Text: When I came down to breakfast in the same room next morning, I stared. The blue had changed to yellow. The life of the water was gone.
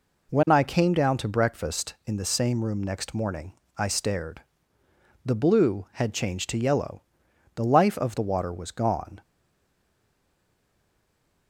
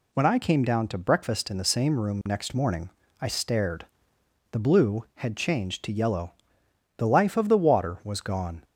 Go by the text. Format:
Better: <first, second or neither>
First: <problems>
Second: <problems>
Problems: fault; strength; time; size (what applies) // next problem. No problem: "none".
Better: second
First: stays silent after the last word; from 9.2 s on; 2.2 s long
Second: none